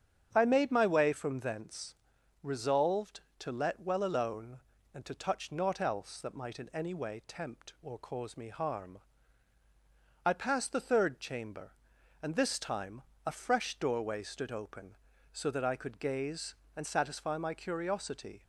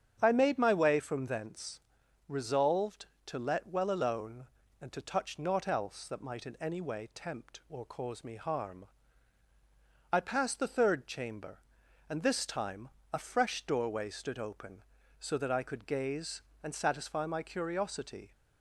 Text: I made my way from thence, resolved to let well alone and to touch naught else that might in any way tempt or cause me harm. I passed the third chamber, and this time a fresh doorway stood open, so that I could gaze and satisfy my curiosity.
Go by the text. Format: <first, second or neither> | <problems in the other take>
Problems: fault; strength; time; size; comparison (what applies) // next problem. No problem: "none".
neither | starts louder than the rest; strong; the same in both // pauses between "time" and "a"; slight; the same in both